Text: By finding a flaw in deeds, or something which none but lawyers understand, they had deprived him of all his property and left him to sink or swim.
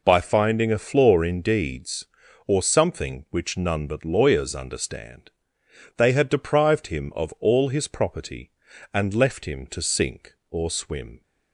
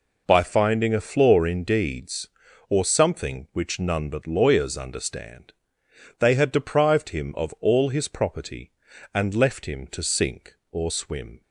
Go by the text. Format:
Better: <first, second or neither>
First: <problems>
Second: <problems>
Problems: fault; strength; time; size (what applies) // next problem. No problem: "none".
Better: neither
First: none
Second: none